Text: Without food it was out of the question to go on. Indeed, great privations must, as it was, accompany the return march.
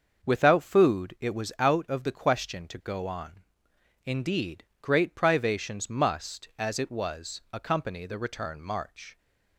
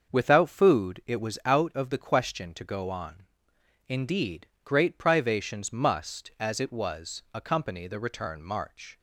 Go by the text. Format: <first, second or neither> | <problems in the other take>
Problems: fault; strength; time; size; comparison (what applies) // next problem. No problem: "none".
neither | starts louder than the rest; the same in both